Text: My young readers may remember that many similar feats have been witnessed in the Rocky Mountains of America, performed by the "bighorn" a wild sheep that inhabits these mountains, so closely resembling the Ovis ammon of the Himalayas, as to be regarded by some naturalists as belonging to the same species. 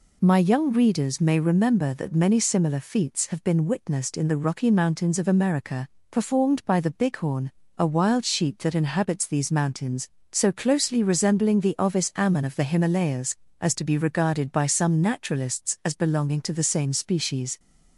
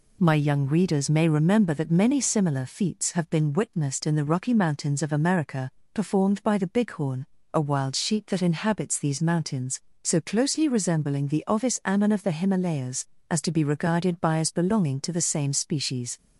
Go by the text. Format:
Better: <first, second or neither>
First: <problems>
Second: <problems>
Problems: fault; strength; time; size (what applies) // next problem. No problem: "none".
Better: first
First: pauses between "bighorn" and "a"; slight; at 7.5 s; 0.24 s long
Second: pauses between "bighorn" and "a"; slight; at 7.2 s; 0.30 s long // skips "some naturalists"; at 14.3 s